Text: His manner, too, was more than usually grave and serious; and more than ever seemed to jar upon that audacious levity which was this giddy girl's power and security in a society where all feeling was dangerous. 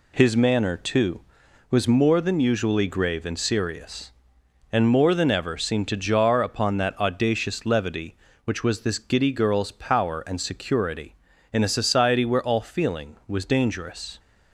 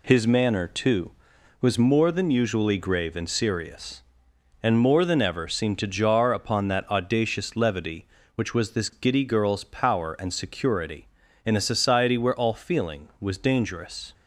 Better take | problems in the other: neither | none

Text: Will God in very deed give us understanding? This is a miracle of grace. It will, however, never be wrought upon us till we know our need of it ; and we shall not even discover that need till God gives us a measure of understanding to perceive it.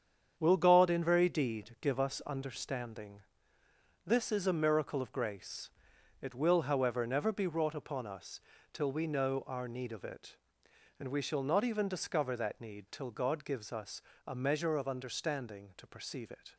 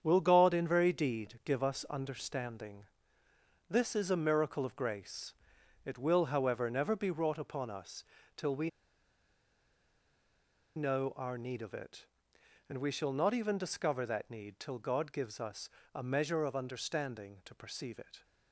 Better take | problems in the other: first | starts louder than the rest; strong; until 1.0 s; 8 dB; strong in the first // pauses between "us" and "till"; slight; at 8.0 s; 0.32 s long; slight in the first // pauses between "we" and "know"; strong; at 8.6 s; 2.0 s long // pauses between "us" and "a"; slight; at 15.6 s; 0.24 s long; slight in the first

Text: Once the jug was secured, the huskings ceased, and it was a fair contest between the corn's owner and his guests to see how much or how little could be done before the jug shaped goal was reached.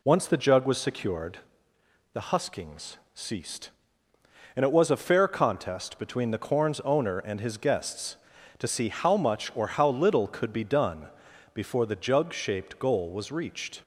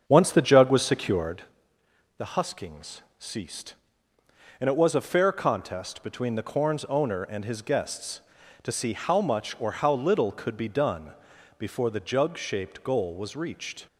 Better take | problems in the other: first | starts louder than the rest; strong; until 1.4 s; 7.5 dB // pauses between "huskings" and "ceased"; slight; at 3.0 s; 0.18 s long; slight in the first // pauses between "done" and "before"; at 11.1 s; 0.44 s long; also in the first

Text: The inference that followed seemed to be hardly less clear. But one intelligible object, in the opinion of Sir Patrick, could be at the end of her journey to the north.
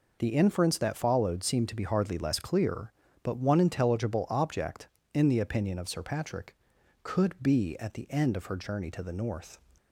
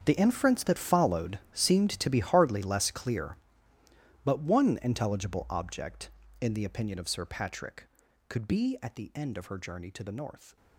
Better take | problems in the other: first | gets quieter; strong; throughout; 15.5 dB // pauses between "followed" and "seemed"; slight; at 1.3 s; 0.16 s long

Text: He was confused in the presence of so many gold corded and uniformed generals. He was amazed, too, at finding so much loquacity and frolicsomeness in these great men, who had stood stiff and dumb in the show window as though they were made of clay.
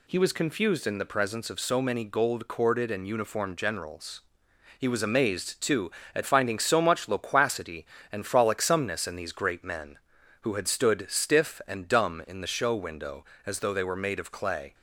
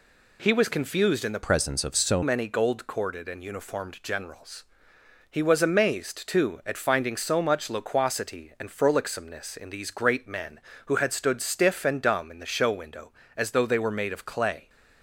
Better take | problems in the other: first | changes voice from "presence" to "so"; from 1.4 to 2.2 s; 0.8 s long

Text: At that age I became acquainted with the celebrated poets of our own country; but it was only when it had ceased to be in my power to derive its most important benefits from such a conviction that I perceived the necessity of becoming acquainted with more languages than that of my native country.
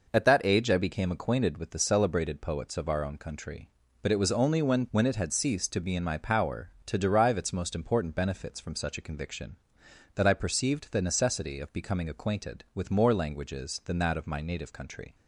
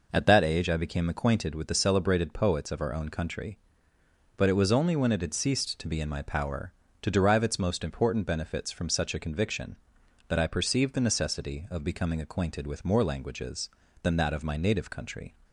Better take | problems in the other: second | says "when" twice; at 4.9 s

